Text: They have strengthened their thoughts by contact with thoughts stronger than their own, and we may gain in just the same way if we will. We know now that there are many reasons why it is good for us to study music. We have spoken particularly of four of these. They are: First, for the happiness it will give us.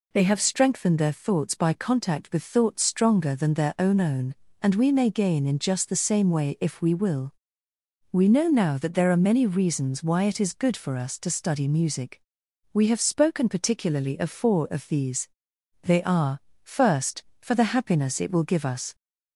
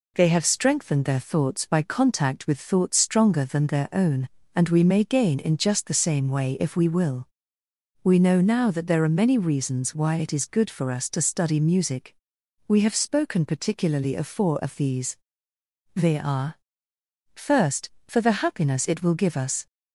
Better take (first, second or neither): second